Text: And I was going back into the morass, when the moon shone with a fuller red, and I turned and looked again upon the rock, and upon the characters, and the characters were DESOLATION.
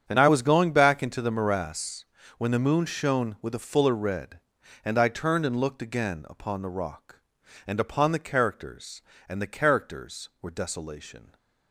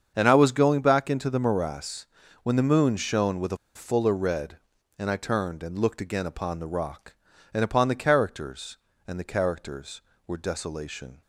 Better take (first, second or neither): first